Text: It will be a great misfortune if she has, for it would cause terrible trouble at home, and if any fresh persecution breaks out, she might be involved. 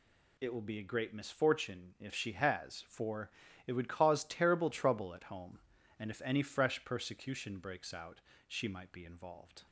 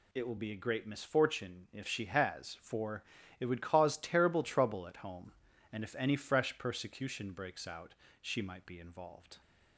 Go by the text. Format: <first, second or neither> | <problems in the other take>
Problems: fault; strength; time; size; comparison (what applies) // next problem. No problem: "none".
neither | pauses between "for" and "it"; slight; the same in both